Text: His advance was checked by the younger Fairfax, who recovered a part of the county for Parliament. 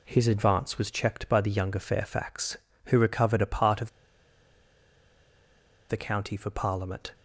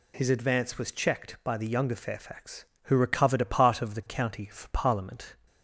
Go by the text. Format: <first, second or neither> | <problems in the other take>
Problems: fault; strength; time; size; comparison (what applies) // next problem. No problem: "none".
second | pauses between "of" and "the"; strong; at 3.8 s; 1.9 s long